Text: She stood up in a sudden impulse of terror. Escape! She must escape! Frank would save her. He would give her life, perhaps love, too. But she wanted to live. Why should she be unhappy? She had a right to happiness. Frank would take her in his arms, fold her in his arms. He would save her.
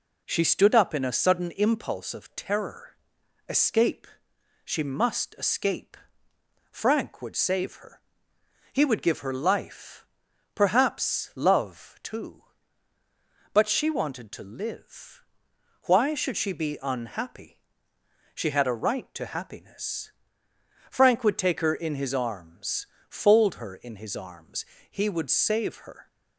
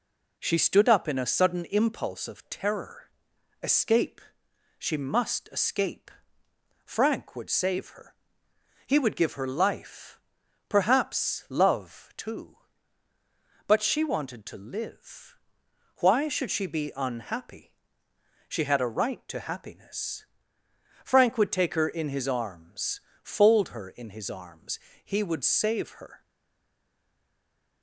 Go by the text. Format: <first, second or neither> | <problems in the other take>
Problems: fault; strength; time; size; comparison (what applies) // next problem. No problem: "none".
first | stays silent after the last word; noticeable; from 26.2 s on; 1.6 s long